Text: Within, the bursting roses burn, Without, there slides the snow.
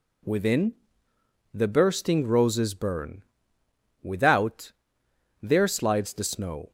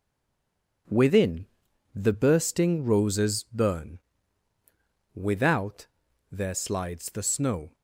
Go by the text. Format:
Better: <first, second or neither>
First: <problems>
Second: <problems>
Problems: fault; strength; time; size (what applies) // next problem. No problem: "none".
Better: first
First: none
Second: stays silent before the first word; slight; until 0.8 s; 0.8 s long